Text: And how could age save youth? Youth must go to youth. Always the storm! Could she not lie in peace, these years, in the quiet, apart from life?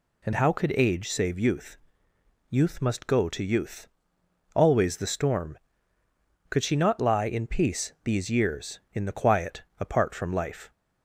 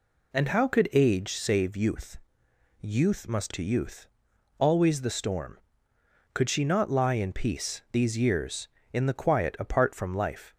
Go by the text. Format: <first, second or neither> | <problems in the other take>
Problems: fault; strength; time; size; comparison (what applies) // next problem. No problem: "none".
first | skips "go"; at 3.5 s